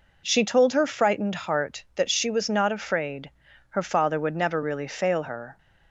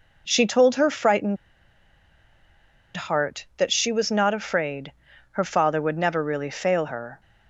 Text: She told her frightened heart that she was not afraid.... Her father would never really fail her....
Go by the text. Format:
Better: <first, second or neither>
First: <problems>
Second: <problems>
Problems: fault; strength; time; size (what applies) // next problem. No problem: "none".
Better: first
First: none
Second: pauses between "frightened" and "heart"; strong; at 1.3 s; 1.5 s long